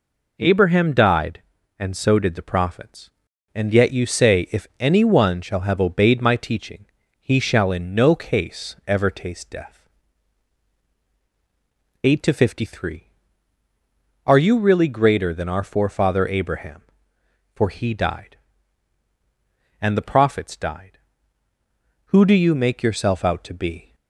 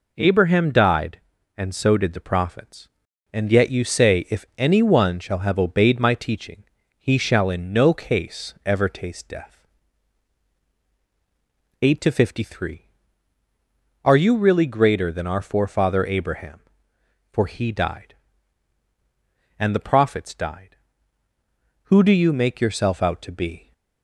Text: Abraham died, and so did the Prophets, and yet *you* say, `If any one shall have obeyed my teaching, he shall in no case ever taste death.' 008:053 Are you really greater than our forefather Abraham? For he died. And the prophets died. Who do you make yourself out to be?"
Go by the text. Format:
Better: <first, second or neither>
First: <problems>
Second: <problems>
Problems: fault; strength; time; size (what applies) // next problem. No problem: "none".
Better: neither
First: none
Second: none